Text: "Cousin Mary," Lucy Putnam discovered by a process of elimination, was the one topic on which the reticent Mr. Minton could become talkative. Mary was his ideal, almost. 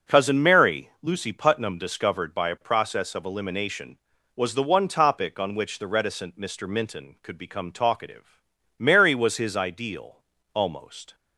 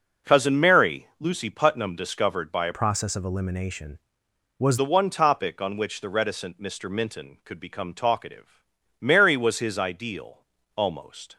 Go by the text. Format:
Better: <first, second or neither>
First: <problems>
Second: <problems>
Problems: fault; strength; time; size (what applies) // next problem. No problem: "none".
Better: first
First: none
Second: changes voice from "process" to "was"; from 2.7 to 4.7 s; 2.0 s long